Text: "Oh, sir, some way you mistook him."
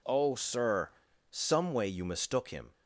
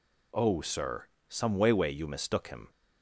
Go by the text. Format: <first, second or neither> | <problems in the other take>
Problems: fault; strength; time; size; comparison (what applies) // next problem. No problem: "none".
first | says "way" twice; at 1.7 s